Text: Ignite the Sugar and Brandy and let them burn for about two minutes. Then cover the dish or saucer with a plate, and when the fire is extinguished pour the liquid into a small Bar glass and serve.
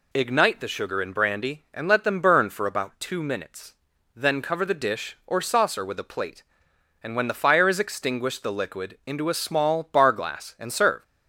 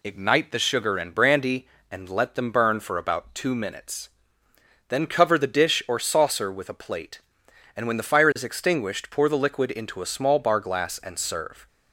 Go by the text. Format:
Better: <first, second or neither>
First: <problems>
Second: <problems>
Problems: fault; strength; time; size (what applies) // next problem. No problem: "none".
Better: second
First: skips "pour"; at 8.4 s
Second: none